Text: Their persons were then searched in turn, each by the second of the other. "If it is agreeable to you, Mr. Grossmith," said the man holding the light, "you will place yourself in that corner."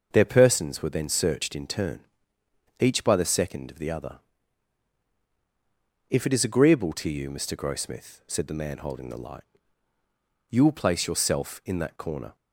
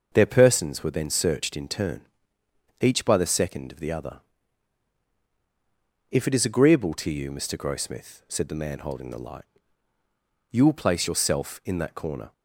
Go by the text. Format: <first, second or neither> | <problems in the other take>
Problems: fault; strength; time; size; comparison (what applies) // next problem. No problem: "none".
neither | starts louder than the rest; noticeable; the same in both